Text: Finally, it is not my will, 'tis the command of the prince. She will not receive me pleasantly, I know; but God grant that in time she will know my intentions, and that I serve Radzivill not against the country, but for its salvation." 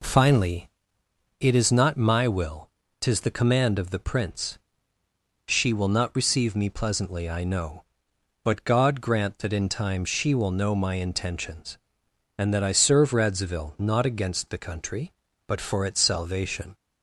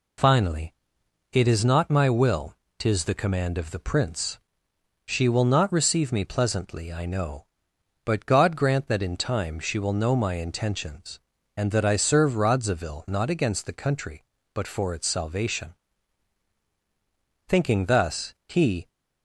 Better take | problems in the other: first | goes on to say "Thinking thus he"; from 17.4 s on; 1.4 s long

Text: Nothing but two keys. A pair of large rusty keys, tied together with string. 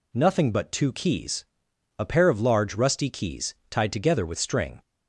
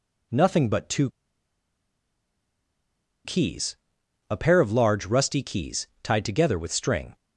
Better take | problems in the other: first | pauses between "two" and "keys"; strong; at 1.0 s; 2.1 s long

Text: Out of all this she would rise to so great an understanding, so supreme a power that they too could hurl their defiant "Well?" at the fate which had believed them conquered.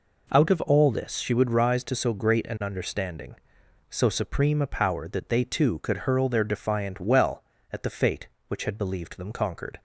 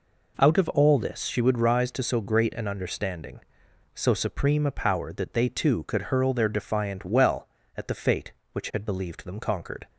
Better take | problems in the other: neither | none

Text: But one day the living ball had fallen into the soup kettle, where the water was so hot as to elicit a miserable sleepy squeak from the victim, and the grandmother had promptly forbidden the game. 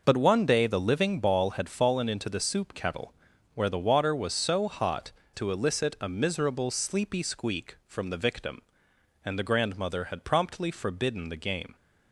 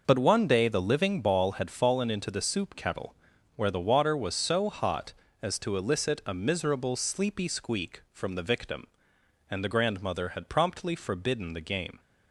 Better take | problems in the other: second | skips "as"; at 5.2 s

